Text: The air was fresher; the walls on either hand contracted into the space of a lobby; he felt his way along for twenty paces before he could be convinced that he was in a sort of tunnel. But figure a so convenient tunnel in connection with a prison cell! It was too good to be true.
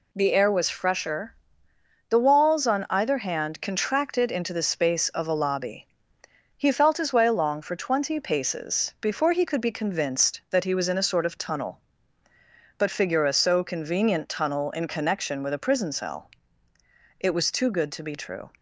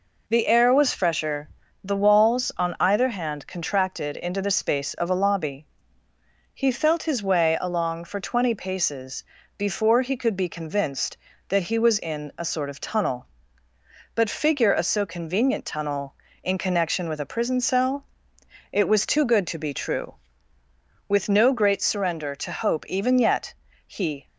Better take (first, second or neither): first